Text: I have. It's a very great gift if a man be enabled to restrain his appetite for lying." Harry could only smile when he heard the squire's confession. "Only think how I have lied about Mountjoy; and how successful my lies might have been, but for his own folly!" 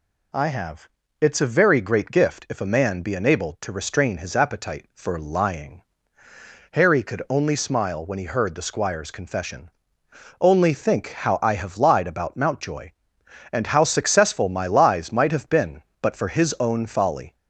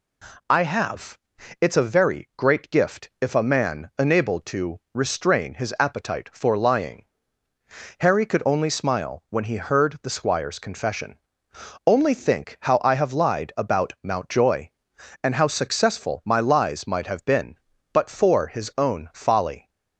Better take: first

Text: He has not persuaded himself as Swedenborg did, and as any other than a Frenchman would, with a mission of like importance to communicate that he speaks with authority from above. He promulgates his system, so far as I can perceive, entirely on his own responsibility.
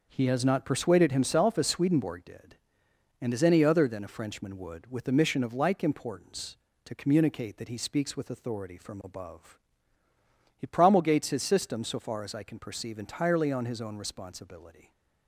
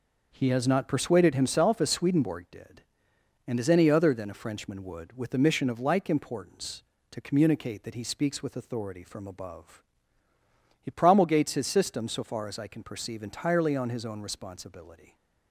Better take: neither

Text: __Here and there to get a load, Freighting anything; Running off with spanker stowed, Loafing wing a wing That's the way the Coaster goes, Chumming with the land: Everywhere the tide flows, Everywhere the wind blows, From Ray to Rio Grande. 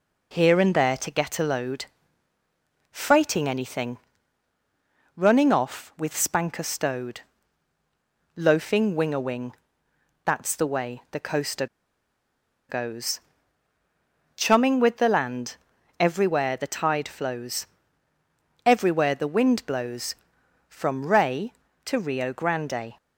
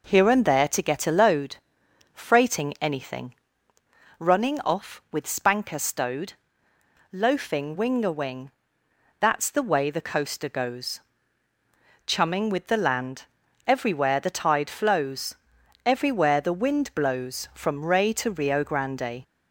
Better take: second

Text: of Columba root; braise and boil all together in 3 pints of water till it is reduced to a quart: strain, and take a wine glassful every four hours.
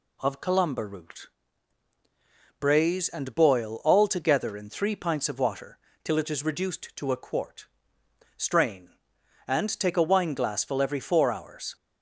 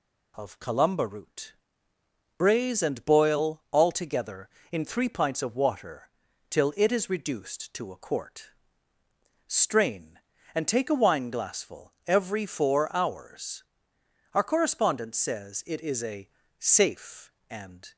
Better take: first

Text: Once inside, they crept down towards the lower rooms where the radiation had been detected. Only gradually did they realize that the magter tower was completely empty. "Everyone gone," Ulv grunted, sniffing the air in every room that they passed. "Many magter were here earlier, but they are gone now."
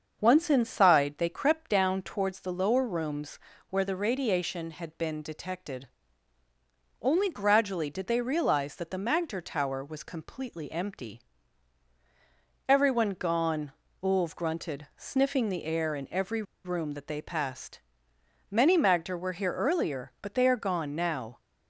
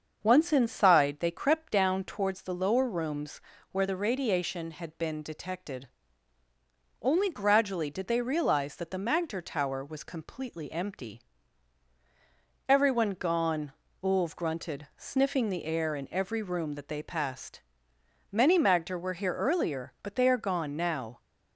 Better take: second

